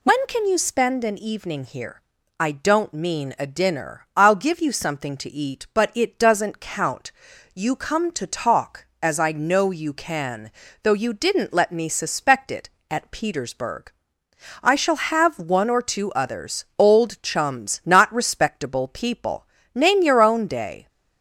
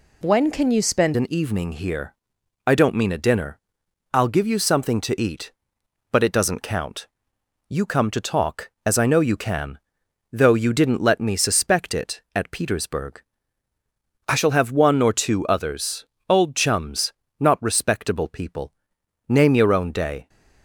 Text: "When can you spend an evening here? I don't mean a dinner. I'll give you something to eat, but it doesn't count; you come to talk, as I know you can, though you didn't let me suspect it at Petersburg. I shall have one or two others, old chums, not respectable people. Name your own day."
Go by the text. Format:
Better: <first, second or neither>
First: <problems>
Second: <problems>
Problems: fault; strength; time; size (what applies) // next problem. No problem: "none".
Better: first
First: none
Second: changes voice at "an"; from 1.1 s on; 19.1 s long